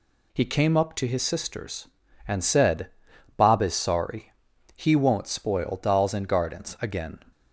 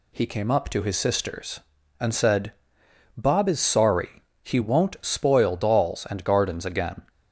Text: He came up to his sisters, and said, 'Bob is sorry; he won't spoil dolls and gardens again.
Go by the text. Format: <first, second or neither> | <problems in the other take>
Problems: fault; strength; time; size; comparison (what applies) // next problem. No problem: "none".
neither | none